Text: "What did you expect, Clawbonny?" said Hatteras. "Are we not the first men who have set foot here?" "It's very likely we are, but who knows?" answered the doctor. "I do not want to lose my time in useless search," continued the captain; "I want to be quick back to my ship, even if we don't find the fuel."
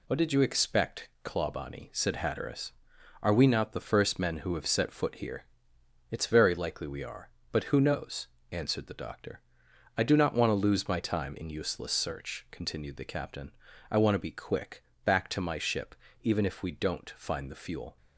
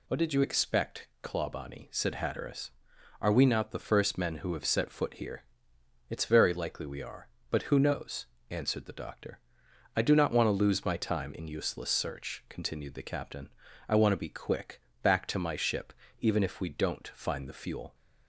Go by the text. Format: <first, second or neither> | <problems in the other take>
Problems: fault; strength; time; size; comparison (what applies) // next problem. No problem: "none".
second | gets quieter; noticeable; throughout; 5.5 dB // pauses between "quick" and "back"; slight; at 14.8 s; 0.22 s long; slight in the second